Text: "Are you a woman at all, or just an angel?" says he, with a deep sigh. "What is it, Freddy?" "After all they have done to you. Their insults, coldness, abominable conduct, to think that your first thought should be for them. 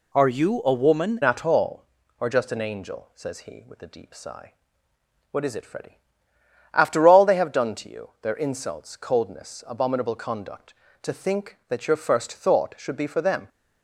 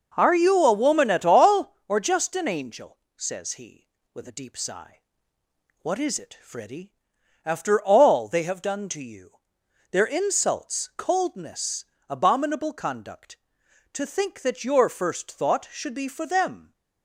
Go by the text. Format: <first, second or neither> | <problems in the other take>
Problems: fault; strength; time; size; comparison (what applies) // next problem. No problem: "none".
second | changes voice at "at"; from 1.2 s on; 12.2 s long